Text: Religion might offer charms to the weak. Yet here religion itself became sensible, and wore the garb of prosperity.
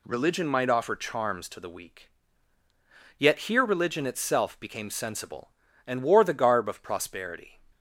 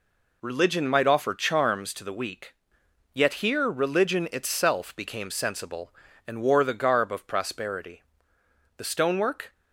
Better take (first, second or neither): first